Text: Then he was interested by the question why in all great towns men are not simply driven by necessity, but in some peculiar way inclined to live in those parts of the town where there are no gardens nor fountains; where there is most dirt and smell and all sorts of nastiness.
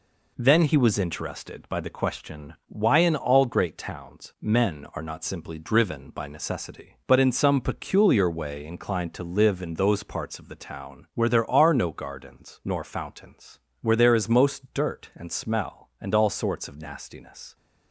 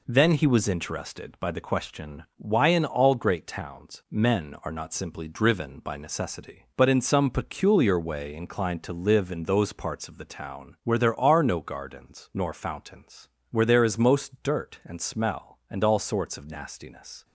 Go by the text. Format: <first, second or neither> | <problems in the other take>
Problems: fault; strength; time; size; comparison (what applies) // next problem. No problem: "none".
neither | none